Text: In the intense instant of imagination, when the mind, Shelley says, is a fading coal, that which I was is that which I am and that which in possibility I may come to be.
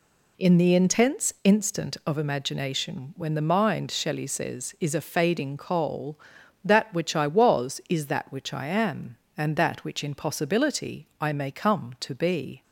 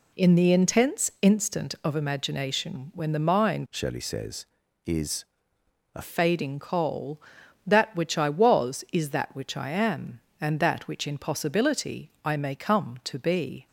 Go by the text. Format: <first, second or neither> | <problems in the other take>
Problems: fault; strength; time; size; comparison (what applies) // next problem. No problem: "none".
first | changes voice from "Shelley" to "a"; from 3.6 to 6.0 s; 2.4 s long // pauses between "is" and "a"; noticeable; at 5.2 s; 0.68 s long